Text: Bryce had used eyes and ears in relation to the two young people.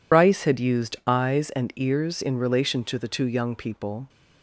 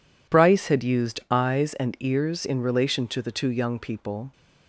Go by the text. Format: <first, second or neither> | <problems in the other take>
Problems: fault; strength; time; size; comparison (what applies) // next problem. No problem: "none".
second | loses the start of "Bryce"; at 0.1 s; 60 ms